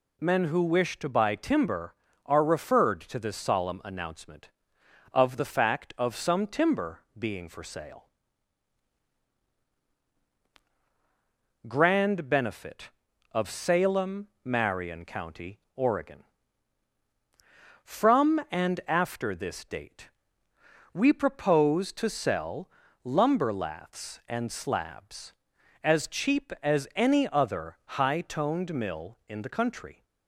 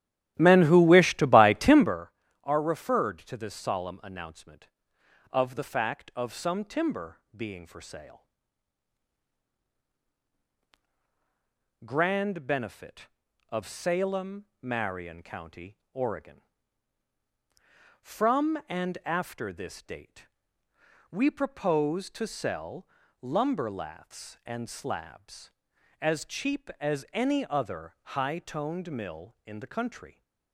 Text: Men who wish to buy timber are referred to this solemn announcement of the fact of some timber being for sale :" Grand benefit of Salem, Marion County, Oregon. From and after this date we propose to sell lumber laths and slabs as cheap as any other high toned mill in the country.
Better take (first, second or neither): first